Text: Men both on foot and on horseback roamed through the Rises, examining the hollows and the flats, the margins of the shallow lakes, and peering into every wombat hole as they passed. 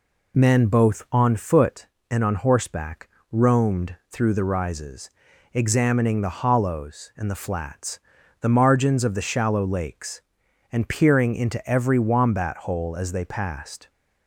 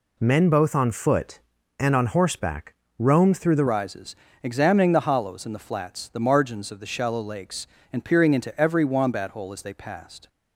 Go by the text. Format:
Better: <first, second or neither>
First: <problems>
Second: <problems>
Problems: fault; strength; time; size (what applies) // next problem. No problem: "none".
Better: first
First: pauses between "horseback" and "roamed"; slight; at 3.0 s; 0.22 s long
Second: pauses between "horseback" and "roamed"; slight; at 2.7 s; 0.24 s long // changes voice at "Rises"; from 3.6 s on; 6.6 s long